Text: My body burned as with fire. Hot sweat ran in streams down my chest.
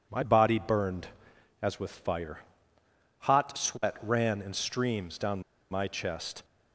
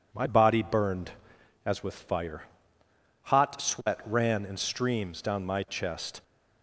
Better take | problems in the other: second | pauses between "down" and "my"; slight; at 5.4 s; 0.28 s long

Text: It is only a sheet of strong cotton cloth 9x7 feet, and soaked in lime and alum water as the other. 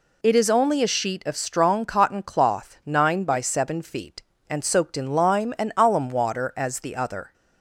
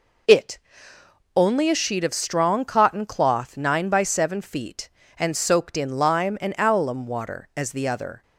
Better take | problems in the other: first | skips "is"; at 0.9 s

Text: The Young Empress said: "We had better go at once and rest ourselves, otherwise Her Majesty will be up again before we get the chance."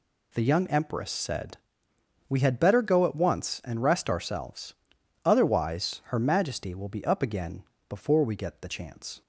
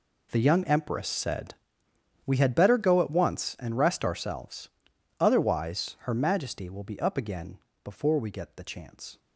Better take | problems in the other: first | gets quieter; strong; throughout; 15.5 dB // pauses between "again" and "before"; slight; at 7.5 s; 0.26 s long; slight in the first

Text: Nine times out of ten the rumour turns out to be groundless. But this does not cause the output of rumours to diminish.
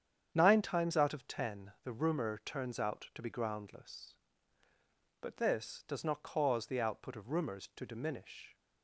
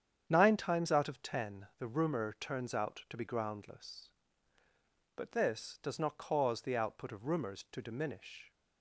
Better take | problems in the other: neither | starts louder than the rest; strong; the same in both

